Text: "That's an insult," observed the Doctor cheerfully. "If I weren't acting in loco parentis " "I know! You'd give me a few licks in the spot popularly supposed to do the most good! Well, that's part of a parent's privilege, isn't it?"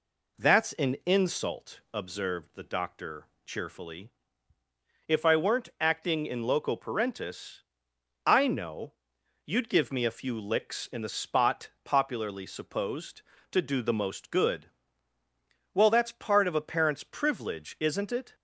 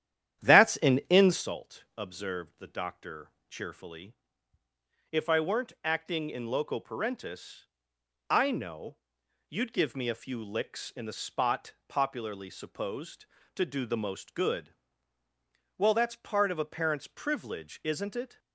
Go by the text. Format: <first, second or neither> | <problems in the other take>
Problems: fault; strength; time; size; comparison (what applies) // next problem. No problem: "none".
first | starts louder than the rest; strong; until 1.4 s; 10.5 dB // pauses between "Doctor" and "cheerfully"; slight; at 3.3 s; 0.16 s long; slight in the first // pauses between "spot" and "popularly"; slight; at 11.7 s; 0.16 s long; slight in the first